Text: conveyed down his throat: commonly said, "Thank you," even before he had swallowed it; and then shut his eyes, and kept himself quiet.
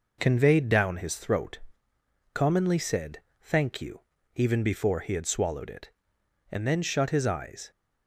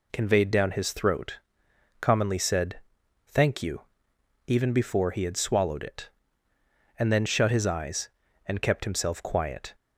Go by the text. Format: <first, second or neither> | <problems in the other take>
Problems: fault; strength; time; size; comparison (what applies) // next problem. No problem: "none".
second | stops before "and kept himself quiet"; at 7.7 s